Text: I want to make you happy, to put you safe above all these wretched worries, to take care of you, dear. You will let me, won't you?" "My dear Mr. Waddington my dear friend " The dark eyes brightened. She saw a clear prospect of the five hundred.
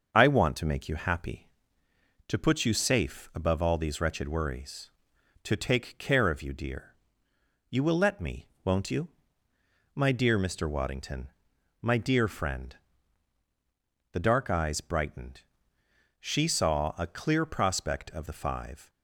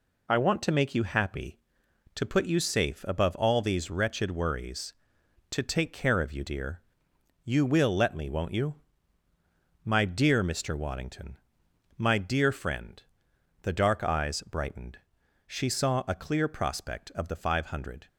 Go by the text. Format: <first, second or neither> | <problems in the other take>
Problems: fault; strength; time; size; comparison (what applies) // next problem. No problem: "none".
second | starts louder than the rest; until 1.1 s; 6.5 dB // pauses between "Waddington" and "my"; noticeable; at 11.2 s; 0.54 s long; noticeable in the second // stops before "hundred"; at 18.8 s